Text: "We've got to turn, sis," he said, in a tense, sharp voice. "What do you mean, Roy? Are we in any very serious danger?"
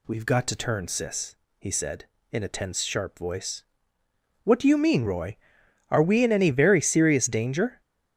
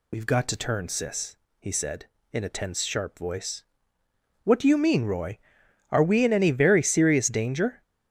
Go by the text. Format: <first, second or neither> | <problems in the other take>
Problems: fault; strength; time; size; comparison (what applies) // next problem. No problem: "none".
first | loses the start of "We've"; at 0.1 s; 55 ms